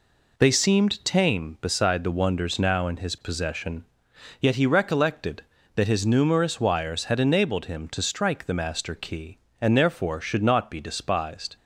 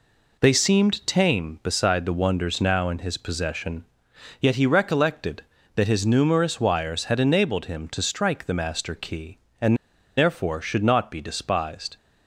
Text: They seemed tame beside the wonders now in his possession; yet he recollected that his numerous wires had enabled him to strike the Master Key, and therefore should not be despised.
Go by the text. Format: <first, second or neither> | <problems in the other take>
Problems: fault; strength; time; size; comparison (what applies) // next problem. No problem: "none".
first | pauses between "and" and "therefore"; at 9.7 s; 0.41 s long